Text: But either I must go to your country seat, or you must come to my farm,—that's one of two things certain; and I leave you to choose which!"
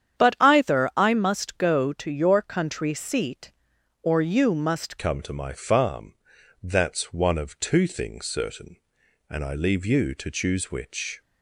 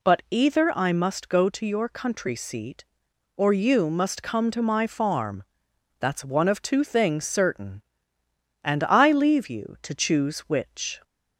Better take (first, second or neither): second